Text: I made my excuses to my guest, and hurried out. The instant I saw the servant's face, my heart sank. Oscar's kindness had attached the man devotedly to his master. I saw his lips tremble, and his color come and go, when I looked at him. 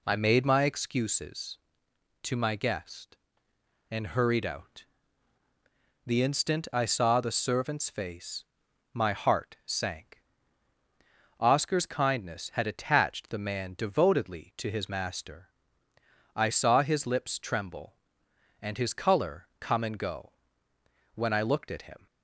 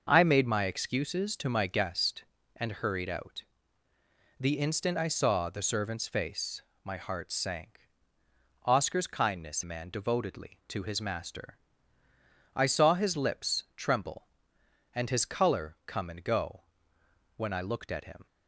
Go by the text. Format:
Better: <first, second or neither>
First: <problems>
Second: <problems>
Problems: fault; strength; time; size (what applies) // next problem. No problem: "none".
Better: first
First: none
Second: starts louder than the rest; noticeable; until 1.1 s; 6 dB // skips "had attached the"; at 9.6 s